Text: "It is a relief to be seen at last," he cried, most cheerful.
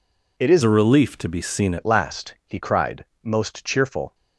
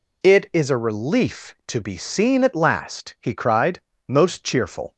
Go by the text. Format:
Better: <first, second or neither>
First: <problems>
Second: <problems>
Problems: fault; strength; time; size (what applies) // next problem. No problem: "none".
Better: second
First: changes voice from "a" to "seen"; from 0.6 to 1.7 s; 1.1 s long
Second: none